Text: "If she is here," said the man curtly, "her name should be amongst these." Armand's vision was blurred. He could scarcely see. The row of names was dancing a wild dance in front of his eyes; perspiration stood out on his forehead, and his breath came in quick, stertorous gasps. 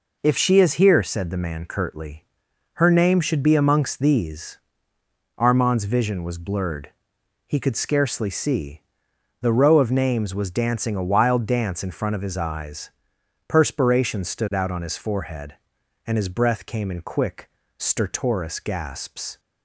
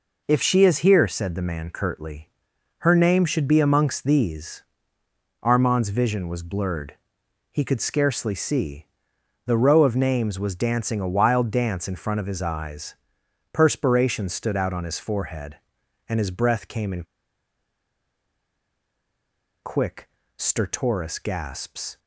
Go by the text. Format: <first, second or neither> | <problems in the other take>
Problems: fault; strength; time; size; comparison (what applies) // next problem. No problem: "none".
first | pauses between "in" and "quick"; strong; at 17.0 s; 2.6 s long